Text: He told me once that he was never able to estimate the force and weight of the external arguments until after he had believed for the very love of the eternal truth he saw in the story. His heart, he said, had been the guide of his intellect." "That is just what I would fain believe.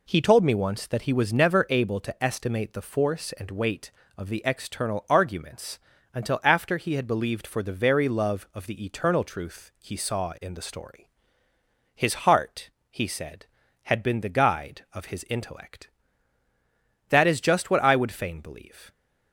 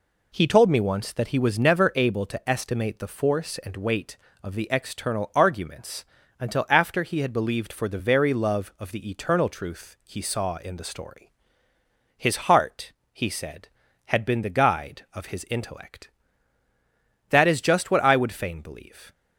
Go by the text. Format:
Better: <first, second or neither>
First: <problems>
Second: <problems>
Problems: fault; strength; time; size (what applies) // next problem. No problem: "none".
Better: neither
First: pauses between "arguments" and "until"; slight; at 5.8 s; 0.34 s long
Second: pauses between "arguments" and "until"; slight; at 6.0 s; 0.34 s long